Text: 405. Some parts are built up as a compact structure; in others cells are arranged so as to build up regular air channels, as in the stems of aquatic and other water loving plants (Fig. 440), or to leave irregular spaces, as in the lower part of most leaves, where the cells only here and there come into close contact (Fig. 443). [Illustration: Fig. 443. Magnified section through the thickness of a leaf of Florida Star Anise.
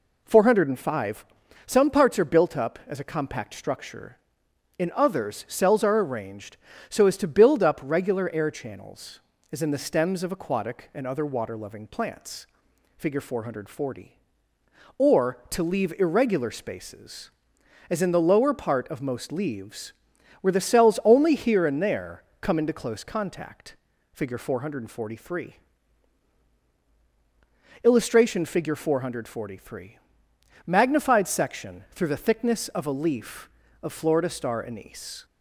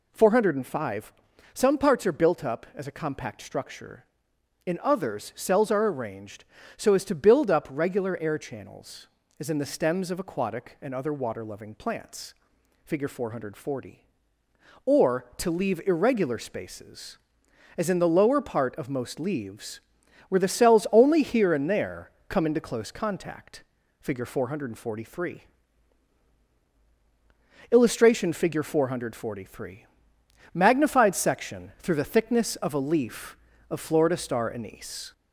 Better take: first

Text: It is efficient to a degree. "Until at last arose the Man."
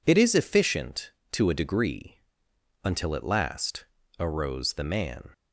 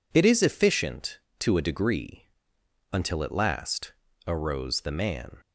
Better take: neither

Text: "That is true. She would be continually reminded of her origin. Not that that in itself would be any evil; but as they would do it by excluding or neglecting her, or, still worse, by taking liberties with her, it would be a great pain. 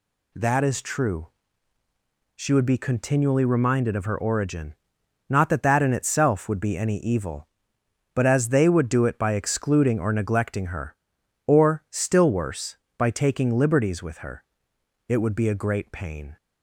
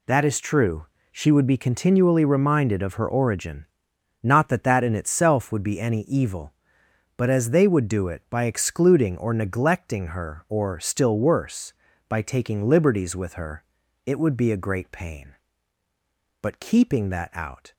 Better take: first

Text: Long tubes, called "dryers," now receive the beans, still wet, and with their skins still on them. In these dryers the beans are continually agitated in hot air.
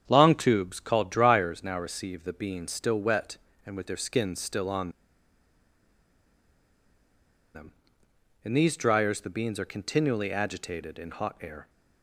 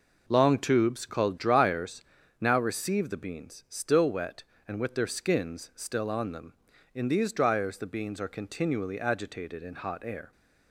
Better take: second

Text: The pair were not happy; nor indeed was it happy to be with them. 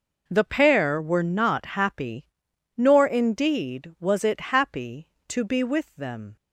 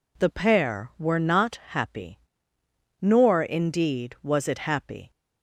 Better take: first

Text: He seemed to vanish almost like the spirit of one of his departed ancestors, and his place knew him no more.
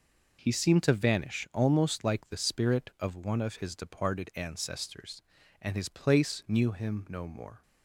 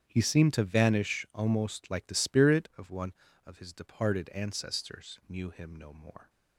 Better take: first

